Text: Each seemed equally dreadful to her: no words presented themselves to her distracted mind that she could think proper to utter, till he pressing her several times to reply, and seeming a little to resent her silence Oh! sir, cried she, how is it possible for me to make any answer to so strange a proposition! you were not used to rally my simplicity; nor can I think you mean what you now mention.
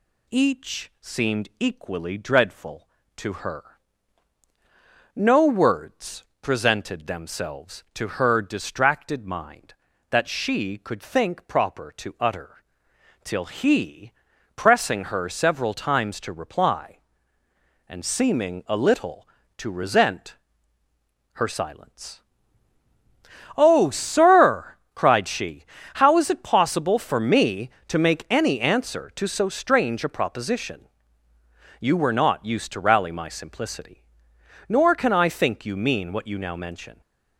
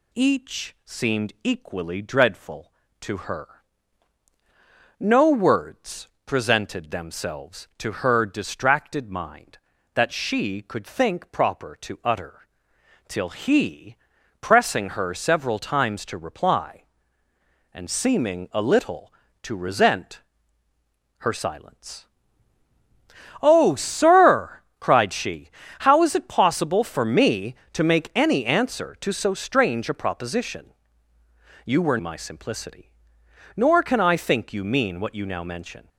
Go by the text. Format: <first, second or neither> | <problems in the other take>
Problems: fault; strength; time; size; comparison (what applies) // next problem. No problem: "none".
first | pauses between "words" and "presented"; slight; at 6.0 s; 0.18 s long; slight in the first // pauses between "he" and "pressing"; noticeable; at 13.9 s; 0.46 s long; also in the first // pauses between "resent" and "her"; noticeable; at 20.2 s; 0.96 s long; noticeable in the first // pauses between "silence" and "Oh"; strong; at 22.0 s; 1.3 s long; strong in the first // skips "not used to rally"; at 31.9 s